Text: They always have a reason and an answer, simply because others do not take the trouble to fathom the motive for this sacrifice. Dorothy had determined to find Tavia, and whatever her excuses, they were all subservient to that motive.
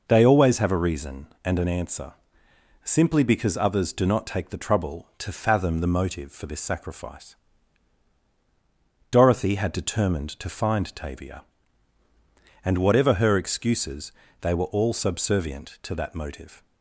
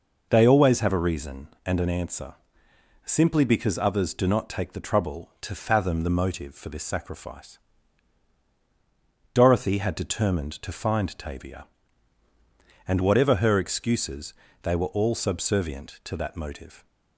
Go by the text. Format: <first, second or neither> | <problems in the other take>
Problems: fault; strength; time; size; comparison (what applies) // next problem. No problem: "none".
neither | none